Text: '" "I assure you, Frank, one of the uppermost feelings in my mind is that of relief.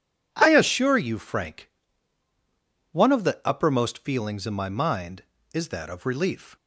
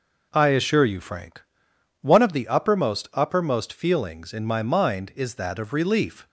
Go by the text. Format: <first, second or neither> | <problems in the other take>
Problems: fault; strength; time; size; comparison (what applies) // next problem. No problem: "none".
first | says "uppermost" twice; at 3.1 s